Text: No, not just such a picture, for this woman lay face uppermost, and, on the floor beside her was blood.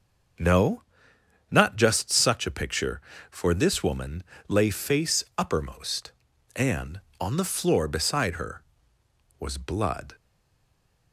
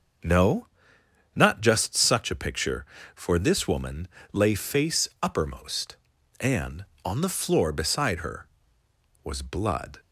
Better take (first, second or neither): second